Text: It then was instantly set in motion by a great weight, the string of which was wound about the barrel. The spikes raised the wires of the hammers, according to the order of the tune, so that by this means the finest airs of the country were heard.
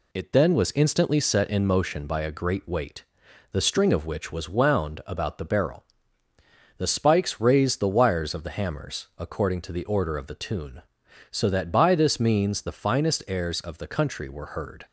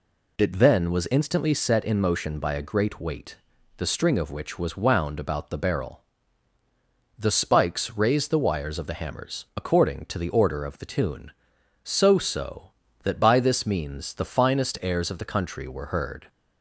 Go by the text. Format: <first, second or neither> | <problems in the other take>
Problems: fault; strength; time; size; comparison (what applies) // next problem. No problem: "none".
first | says "so" twice; at 12.1 s